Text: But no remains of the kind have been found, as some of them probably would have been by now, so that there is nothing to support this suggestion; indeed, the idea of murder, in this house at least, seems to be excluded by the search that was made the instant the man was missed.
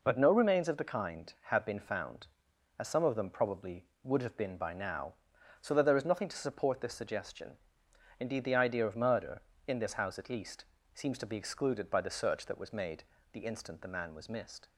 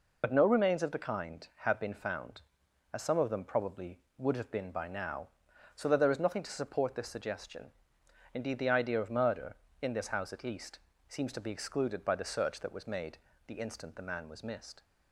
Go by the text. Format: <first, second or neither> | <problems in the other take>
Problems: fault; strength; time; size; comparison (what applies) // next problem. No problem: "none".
first | loses the start of "But"; at 0.2 s; 65 ms // pauses between "made" and "the"; slight; at 13.1 s; 0.30 s long; slight in the first